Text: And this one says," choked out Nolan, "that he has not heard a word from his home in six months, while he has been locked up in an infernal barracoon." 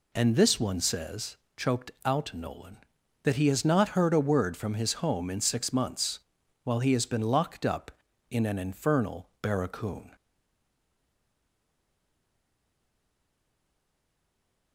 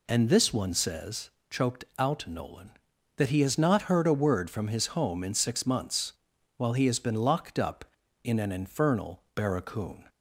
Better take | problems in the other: second | pauses between "choked" and "out"; slight; at 1.9 s; 0.16 s long; slight in the second // stays silent after the last word; strong; from 10.1 s on; 4.6 s long

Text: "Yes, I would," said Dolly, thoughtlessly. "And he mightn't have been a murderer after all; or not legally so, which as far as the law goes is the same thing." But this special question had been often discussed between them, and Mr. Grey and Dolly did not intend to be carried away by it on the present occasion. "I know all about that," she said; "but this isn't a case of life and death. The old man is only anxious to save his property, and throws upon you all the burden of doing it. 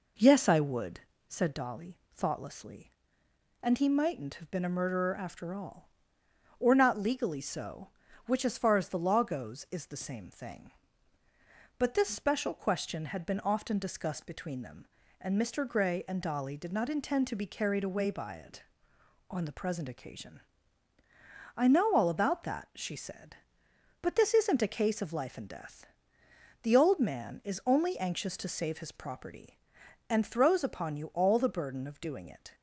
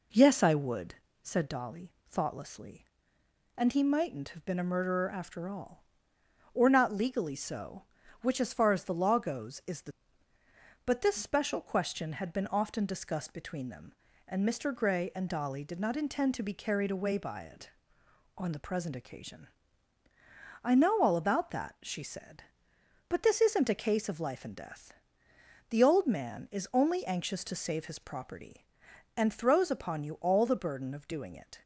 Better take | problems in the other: first | skips "same thing"; at 10.3 s

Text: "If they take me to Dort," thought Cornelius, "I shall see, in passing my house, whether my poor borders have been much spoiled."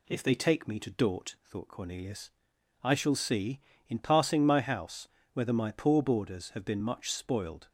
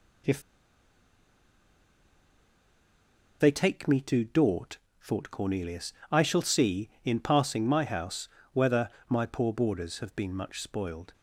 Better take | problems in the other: first | pauses between "If" and "they"; strong; at 0.4 s; 2.9 s long // pauses between "whether" and "my"; slight; at 8.8 s; 0.18 s long

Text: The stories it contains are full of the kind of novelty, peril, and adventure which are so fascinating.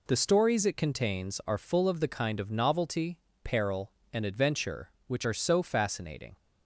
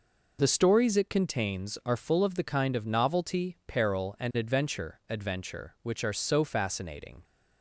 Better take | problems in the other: first | says "adventure" twice; at 5.0 s

